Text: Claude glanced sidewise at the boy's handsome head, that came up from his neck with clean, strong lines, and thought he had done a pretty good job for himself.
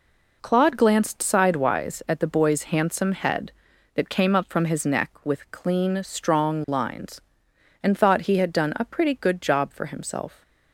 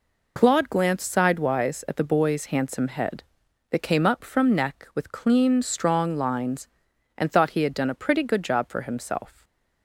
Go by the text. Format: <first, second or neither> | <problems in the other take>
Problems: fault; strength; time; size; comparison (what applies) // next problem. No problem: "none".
first | skips "his"; at 4.5 s // stays silent after the last word; slight; from 9.3 s on; 0.5 s long